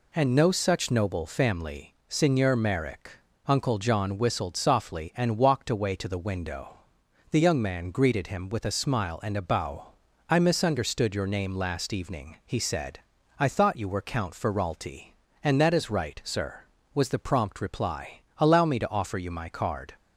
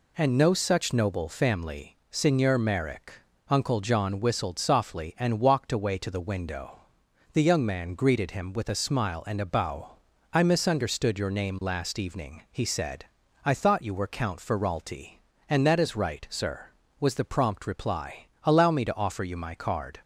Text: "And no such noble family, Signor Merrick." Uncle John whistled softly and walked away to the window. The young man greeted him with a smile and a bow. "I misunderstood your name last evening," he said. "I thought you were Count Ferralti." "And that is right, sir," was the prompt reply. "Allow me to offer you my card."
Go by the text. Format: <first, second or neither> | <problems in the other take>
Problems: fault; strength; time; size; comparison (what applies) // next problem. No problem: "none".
neither | none